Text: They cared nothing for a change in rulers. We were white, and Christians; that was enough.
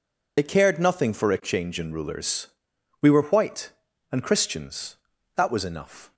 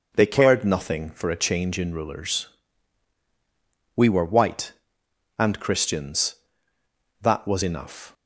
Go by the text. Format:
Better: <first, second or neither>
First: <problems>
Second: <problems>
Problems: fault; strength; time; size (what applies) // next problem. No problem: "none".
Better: second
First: loses the start of "They"; at 0.3 s; 55 ms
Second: none